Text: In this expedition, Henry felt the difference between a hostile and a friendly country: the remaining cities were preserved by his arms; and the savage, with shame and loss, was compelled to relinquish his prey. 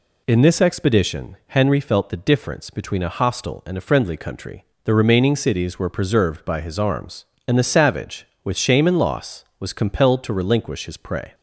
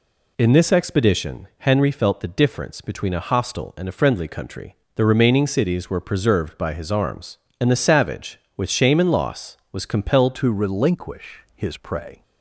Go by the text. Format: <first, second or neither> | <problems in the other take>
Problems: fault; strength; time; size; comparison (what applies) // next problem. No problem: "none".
first | changes voice at "to"; from 10.3 s on; 1.9 s long